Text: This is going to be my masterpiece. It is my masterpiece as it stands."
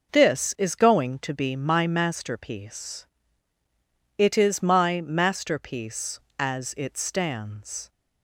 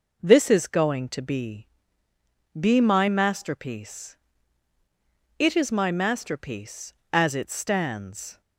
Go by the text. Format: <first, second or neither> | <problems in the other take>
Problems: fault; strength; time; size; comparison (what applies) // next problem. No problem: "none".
first | says "be" twice; at 2.5 s